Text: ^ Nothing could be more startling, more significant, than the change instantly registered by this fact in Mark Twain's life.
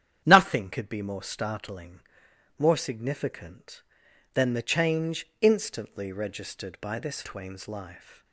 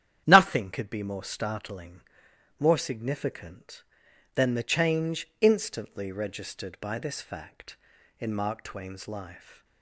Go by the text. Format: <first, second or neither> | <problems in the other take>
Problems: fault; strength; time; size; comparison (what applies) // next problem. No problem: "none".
second | starts louder than the rest; strong; until 1.2 s; 9.5 dB; strong in the second // skips "fact in Mark"; at 7.2 s